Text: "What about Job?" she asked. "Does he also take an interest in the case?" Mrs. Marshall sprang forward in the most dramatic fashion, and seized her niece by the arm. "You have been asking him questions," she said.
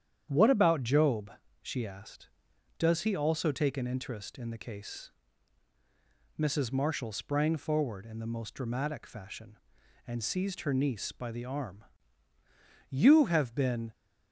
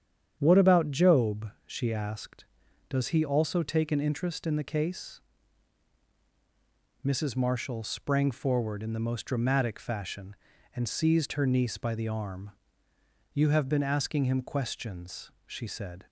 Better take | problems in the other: second | starts louder than the rest; strong; until 1.3 s; 9.5 dB; strong in the second // stops before "asking him questions she said"; at 13.9 s

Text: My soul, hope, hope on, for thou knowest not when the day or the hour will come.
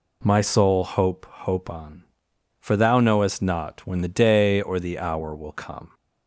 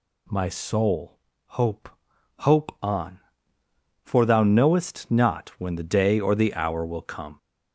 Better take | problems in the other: first | gets louder; noticeable; throughout; 4.5 dB

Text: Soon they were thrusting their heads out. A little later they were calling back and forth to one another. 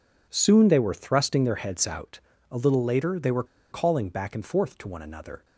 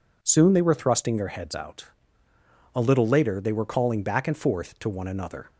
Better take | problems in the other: second | pauses between "were" and "calling"; slight; at 3.4 s; 0.27 s long

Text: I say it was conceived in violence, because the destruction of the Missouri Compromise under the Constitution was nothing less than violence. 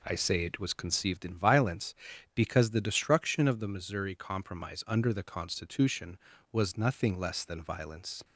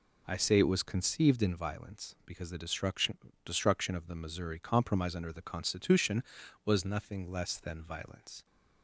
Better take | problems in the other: first | says "destruction" twice; at 3.4 s

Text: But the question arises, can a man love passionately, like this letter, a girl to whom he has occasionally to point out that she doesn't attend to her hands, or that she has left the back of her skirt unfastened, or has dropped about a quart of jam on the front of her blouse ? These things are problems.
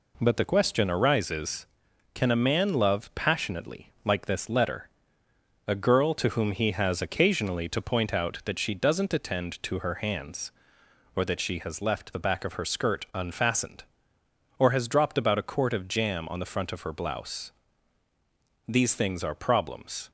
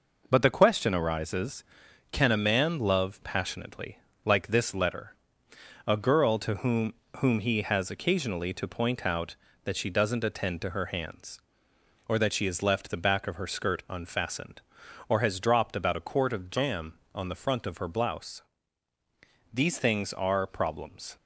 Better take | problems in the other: first | says "whom" twice; at 7.1 s

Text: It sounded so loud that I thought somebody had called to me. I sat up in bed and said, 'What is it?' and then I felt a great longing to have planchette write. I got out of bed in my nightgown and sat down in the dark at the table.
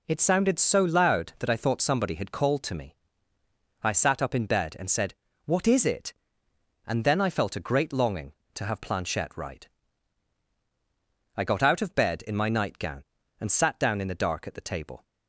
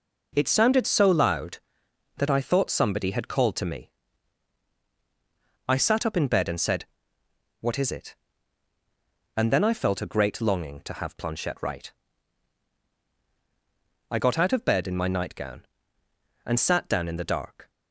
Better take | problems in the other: first | stops before "at the table"; at 17.6 s

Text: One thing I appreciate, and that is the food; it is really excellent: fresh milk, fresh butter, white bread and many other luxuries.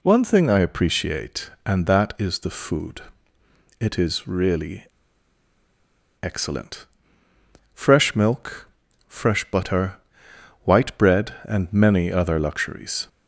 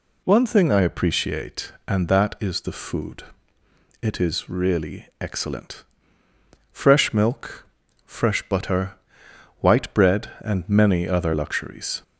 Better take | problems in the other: second | pauses between "really" and "excellent"; strong; at 4.8 s; 1.3 s long

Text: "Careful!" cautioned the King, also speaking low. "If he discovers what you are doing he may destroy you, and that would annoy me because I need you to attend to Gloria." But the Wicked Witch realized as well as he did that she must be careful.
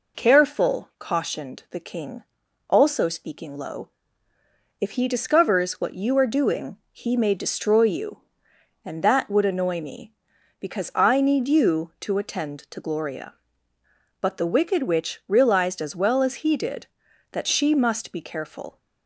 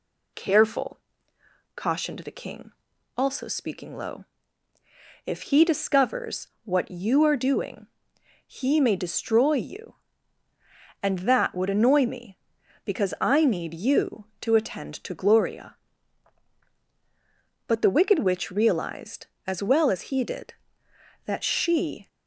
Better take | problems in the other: first | pauses between "discovers" and "what"; slight; at 6.4 s; 0.16 s long // pauses between "doing" and "he"; noticeable; at 7.8 s; 0.62 s long; slight in the first // stops before "must be careful"; at 22.0 s

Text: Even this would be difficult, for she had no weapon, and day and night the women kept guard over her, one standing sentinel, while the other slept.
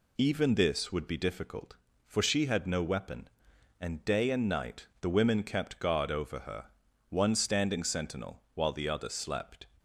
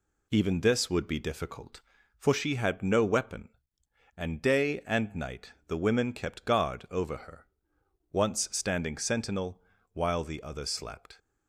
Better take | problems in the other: first | pauses between "night" and "the"; slight; at 5.5 s; 0.16 s long; slight in the first // says "once" for "one"; at 8.1 s

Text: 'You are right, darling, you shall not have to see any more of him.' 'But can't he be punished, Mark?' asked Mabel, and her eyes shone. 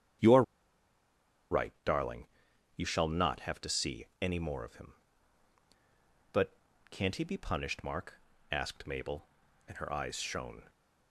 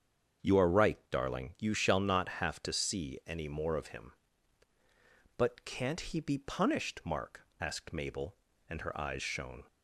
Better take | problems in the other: second | starts louder than the rest; strong; until 2.9 s; 9.5 dB; strong in the second // pauses between "are" and "right"; at 0.4 s; 1.0 s long // pauses between "see" and "any"; slight; at 4.0 s; 0.16 s long // pauses between "But" and "can't"; at 6.5 s; 0.38 s long

